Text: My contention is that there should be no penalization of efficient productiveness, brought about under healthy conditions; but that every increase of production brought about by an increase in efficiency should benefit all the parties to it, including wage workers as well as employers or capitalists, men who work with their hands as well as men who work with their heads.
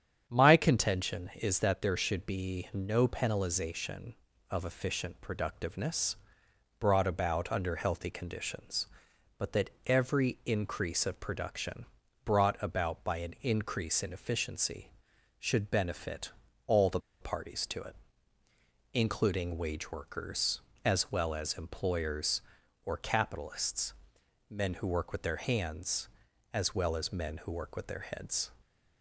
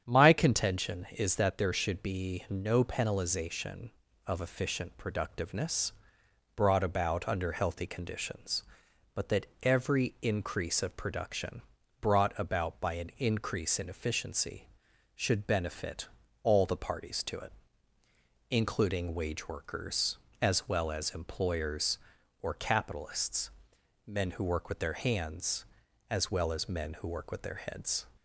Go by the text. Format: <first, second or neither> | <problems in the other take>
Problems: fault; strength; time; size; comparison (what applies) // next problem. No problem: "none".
second | starts louder than the rest; strong; until 1.2 s; 8.5 dB; strong in the second // pauses between "that" and "every"; slight; at 9.6 s; 0.16 s long; slight in the second // pauses between "production" and "brought"; at 11.8 s; 0.40 s long; also in the second // pauses between "benefit" and "all"; slight; at 16.3 s; 0.34 s long; slight in the second // pauses between "the" and "parties"; slight; at 16.9 s; 0.21 s long